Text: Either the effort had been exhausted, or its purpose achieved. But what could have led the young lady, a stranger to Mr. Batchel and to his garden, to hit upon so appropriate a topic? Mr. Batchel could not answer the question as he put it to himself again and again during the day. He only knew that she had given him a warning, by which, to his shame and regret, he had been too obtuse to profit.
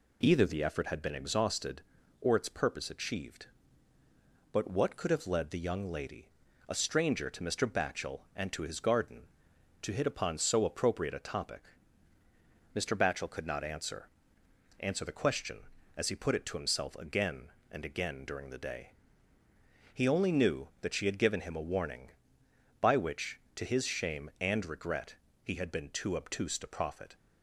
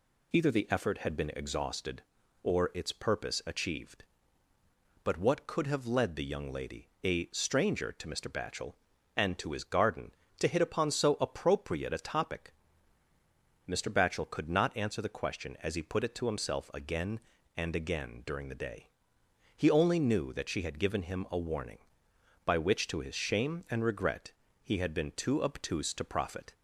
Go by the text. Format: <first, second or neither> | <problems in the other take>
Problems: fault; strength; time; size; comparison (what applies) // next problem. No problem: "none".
second | says "answer" twice; at 14.7 s